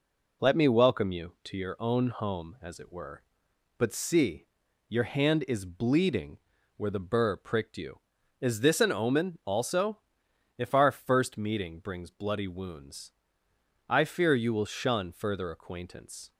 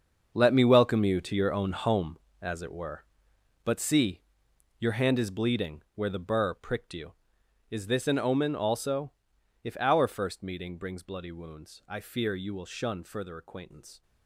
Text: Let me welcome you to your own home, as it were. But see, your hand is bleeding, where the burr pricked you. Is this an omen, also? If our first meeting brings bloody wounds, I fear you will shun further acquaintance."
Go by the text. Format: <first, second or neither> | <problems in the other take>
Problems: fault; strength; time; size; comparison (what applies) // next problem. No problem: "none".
first | gets quieter; strong; throughout; 14 dB